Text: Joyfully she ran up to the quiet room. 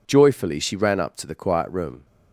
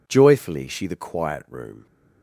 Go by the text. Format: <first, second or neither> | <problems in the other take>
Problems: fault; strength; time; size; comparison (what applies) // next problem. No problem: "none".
first | skips "ran up to"; at 0.8 s